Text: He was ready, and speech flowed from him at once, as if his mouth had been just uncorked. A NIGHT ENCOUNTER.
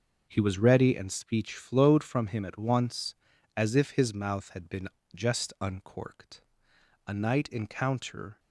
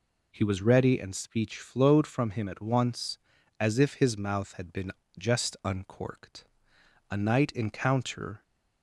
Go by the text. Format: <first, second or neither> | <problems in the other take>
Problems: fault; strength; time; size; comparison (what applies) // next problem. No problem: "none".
second | gets quieter; strong; throughout; 10.5 dB // pauses between "been" and "just"; slight; at 4.8 s; 0.26 s long; slight in the second